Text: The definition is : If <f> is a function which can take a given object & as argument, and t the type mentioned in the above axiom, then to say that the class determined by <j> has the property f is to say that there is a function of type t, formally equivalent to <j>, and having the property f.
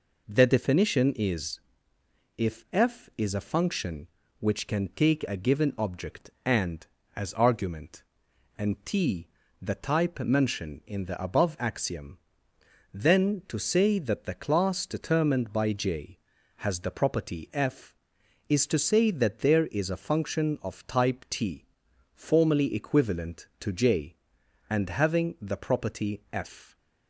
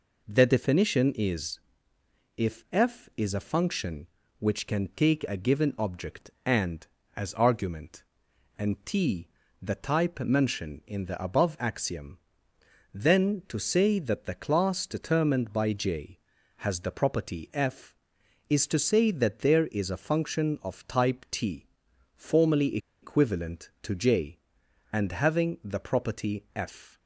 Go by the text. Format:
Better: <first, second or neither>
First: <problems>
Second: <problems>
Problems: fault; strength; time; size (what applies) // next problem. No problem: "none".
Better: first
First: pauses between "t" and "the"; slight; at 9.2 s; 0.34 s long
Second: pauses between "t" and "the"; slight; at 9.2 s; 0.34 s long // pauses between "formally" and "equivalent"; slight; at 22.7 s; 0.24 s long